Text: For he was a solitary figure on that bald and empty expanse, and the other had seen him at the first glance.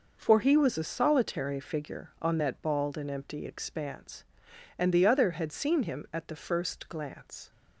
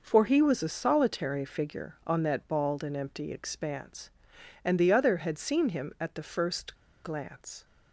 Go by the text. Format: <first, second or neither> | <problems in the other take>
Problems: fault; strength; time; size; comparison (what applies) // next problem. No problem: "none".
first | pauses between "first" and "glance"; slight; at 6.7 s; 0.28 s long